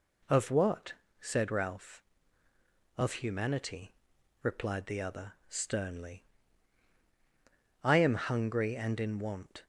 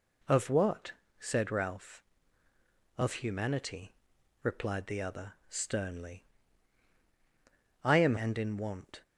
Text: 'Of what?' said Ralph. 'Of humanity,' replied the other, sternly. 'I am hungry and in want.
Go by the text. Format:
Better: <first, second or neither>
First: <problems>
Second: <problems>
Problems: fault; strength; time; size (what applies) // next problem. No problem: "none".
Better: first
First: none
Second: skips "hungry"; at 8.1 s